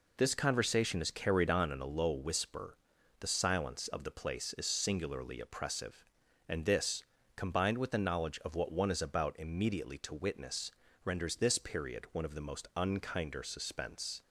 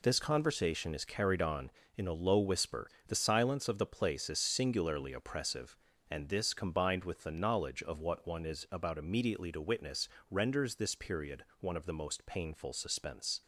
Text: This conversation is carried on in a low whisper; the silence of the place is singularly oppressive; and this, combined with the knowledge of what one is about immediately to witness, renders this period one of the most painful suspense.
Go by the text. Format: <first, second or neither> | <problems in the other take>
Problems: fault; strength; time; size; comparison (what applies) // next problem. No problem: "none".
second | says "unkinder" for "painful"; at 12.7 s